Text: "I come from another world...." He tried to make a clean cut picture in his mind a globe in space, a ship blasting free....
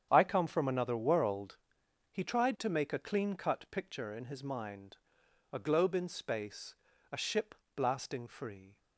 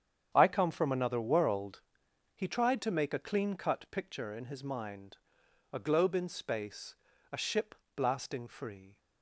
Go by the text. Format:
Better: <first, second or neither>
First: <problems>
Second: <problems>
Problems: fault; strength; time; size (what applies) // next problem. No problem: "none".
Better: neither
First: starts louder than the rest; strong; until 1.1 s; 8.5 dB // pauses between "mind" and "a"; noticeable; at 4.9 s; 0.56 s long // pauses between "ship" and "blasting"; slight; at 7.5 s; 0.22 s long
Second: starts louder than the rest; strong; until 1.3 s; 8 dB // pauses between "mind" and "a"; noticeable; at 5.1 s; 0.56 s long // pauses between "ship" and "blasting"; slight; at 7.7 s; 0.22 s long